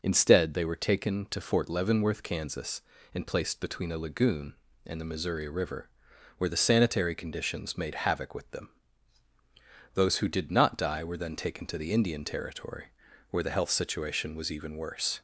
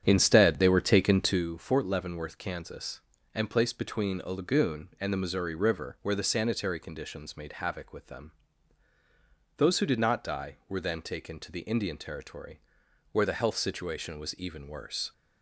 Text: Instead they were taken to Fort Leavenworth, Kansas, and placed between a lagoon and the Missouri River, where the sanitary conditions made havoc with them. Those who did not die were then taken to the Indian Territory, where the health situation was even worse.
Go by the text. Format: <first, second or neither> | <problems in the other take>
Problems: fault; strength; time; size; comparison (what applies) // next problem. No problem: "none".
first | starts louder than the rest; strong; until 1.5 s; 8.5 dB